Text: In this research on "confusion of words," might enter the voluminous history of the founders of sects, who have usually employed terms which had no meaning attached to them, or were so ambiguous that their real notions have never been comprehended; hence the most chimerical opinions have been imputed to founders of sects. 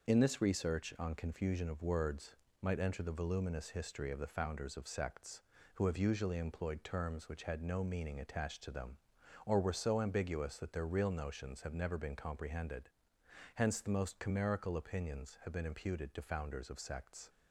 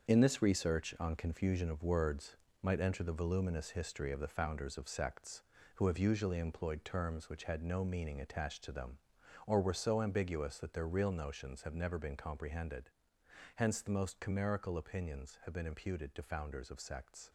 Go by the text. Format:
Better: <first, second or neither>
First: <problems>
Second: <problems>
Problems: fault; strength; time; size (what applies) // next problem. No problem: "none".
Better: first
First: none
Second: gets quieter; strong; throughout; 8 dB